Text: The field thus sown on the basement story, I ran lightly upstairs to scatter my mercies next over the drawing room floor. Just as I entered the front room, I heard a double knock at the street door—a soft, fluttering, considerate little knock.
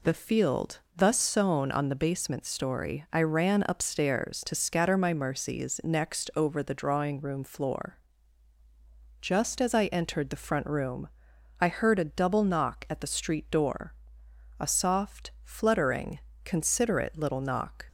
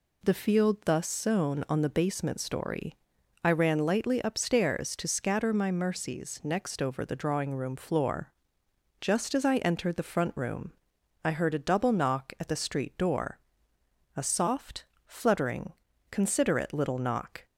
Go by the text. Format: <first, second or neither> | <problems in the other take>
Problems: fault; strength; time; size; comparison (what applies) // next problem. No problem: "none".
second | pauses between "field" and "thus"; slight; at 0.8 s; 0.16 s long // skips "lightly"; at 3.6 s